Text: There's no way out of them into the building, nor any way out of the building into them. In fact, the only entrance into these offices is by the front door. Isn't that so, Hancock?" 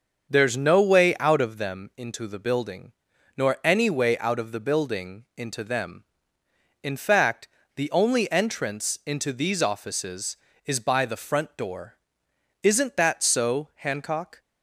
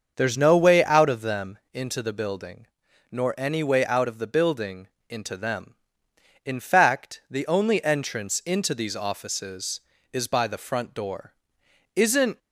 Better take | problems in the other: first | starts louder than the rest; until 1.1 s; 6.5 dB; also in the first // pauses between "building" and "into"; slight; at 4.8 s; 0.20 s long // stops before "that so Hancock"; at 12.3 s

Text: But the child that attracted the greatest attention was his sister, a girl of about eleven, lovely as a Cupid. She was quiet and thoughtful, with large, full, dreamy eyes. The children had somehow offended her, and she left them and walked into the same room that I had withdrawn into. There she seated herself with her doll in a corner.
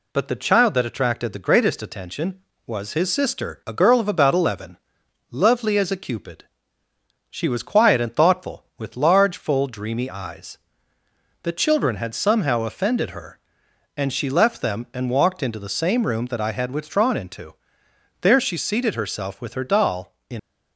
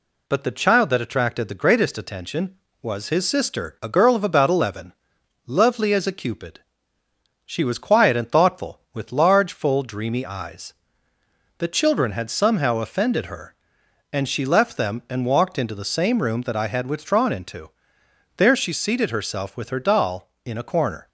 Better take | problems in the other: second | stops before "a corner"; at 20.3 s

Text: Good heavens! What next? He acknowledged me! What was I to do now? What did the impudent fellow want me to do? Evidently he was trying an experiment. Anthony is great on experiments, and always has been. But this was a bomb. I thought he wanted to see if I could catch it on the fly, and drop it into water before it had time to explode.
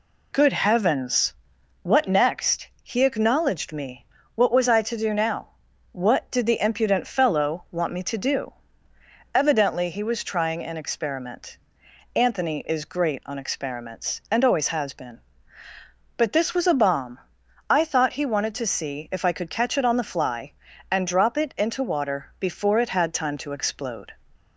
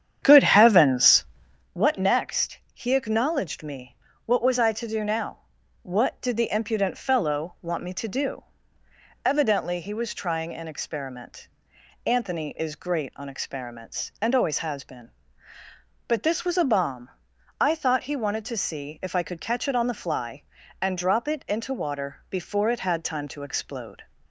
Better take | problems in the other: first | starts louder than the rest; strong; until 1.7 s; 9 dB

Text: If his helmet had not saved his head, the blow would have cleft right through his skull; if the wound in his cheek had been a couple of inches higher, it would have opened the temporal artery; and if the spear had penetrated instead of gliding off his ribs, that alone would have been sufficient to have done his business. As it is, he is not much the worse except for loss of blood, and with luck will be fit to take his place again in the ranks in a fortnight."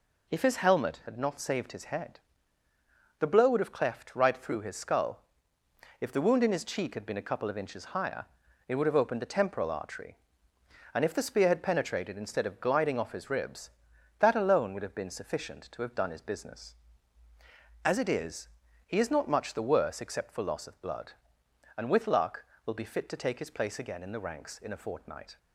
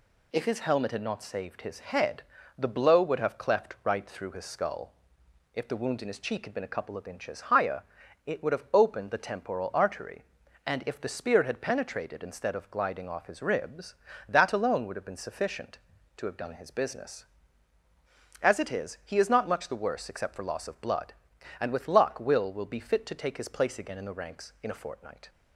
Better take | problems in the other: first | says "will" twice; at 22.5 s

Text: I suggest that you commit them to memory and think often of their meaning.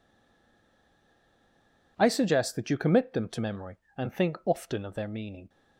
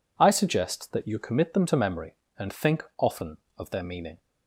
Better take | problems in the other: second | stays silent before the first word; noticeable; until 1.9 s; 1.9 s long

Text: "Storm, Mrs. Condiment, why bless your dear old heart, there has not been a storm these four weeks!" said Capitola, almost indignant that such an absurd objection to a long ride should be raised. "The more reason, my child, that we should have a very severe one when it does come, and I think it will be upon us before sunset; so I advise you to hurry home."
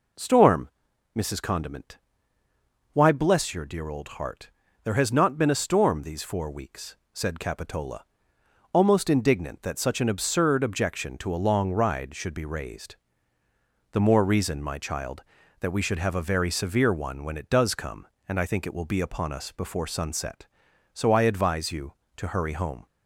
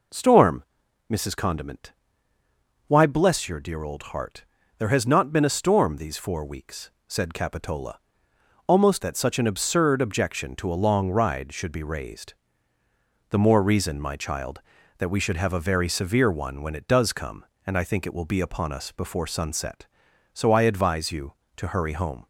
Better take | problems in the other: first | skips "indignant"; at 9.0 s

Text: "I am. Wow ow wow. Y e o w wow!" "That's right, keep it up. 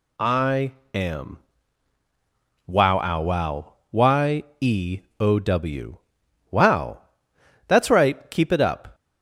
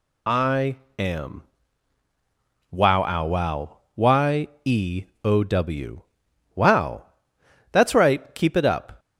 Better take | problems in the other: first | loses the start of "I"; at 0.2 s; 35 ms // pauses between "I" and "am"; slight; at 0.7 s; 0.24 s long; slight in the first // pauses between "Y" and "e"; slight; at 4.4 s; 0.18 s long; slight in the first // pauses between "e" and "o"; slight; at 5.0 s; 0.20 s long; slight in the first // pauses between "w" and "wow"; noticeable; at 6.0 s; 0.54 s long; noticeable in the first

